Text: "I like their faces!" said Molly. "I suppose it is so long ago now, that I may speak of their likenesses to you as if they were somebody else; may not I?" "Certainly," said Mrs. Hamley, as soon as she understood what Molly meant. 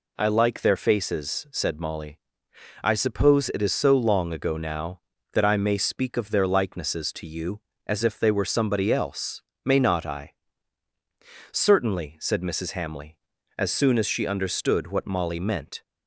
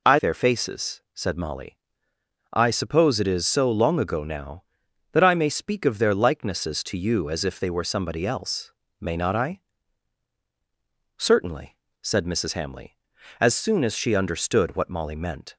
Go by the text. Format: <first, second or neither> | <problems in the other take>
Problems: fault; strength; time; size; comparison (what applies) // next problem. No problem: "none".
first | skips "like"; at 0.1 s